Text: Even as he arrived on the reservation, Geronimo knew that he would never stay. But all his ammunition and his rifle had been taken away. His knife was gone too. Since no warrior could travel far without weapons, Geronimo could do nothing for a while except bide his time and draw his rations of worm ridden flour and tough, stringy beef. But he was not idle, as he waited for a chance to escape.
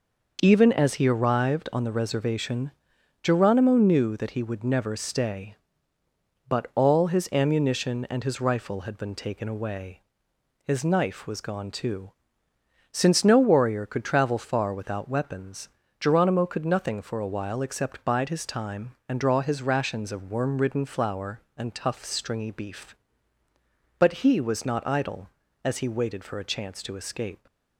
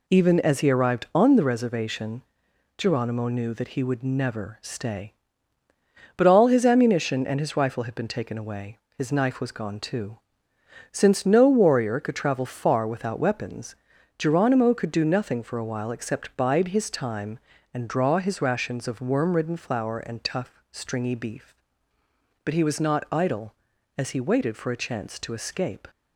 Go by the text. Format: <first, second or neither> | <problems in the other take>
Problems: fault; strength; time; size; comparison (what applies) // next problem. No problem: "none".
second | skips "do"; at 16.6 s